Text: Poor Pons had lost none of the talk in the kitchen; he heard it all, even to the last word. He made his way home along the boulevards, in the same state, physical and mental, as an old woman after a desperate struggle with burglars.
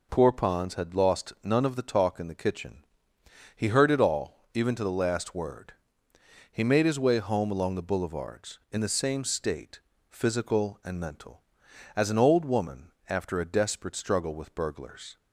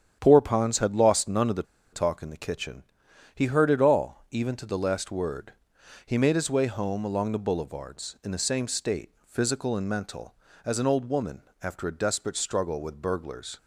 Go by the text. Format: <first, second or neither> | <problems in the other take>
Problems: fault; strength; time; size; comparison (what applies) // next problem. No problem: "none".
first | starts louder than the rest; strong; until 1.2 s; 9.5 dB // pauses between "the" and "talk"; slight; at 1.6 s; 0.29 s long // pauses between "woman" and "after"; slight; at 11.4 s; 0.20 s long; slight in the first